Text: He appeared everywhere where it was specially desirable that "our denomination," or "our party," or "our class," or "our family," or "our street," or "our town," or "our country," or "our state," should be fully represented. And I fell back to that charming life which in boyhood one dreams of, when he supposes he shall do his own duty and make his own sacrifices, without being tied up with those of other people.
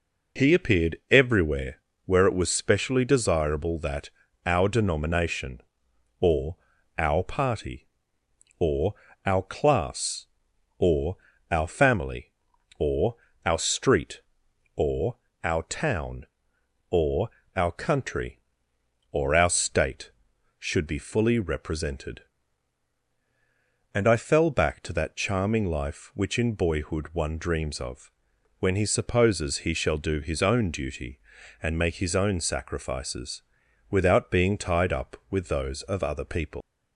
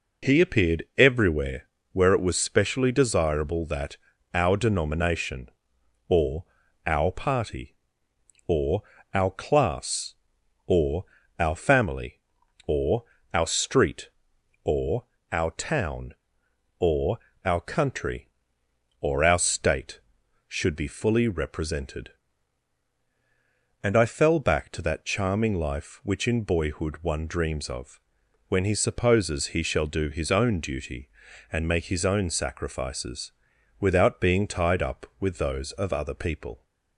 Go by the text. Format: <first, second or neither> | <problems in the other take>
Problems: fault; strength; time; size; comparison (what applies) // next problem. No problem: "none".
second | pauses between "everywhere" and "where"; slight; at 1.8 s; 0.24 s long; slight in the second // pauses between "that" and "our"; slight; at 4.1 s; 0.34 s long; slight in the second // pauses between "or" and "our"; at 6.5 s; 0.40 s long; also in the second // pauses between "or" and "our"; slight; at 8.9 s; 0.30 s long; slight in the second // pauses between "or" and "our"; slight; at 11.1 s; 0.34 s long; slight in the second // pauses between "or" and "our"; slight; at 13.1 s; 0.30 s long; slight in the second // pauses between "or" and "our"; slight; at 15.1 s; 0.26 s long; slight in the second // pauses between "or" and "our"; slight; at 17.2 s; 0.26 s long; slight in the second // leaves "people" unfinished; at 36.6 s; 145 ms